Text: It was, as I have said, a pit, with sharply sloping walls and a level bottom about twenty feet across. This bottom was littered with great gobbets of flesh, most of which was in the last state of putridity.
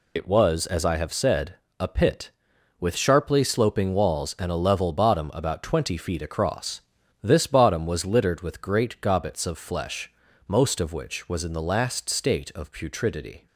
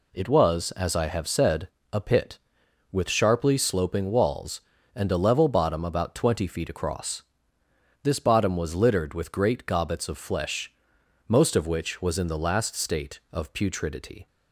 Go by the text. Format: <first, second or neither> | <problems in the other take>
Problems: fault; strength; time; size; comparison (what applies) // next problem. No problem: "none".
second | loses the start of "It"; at 0.1 s; 90 ms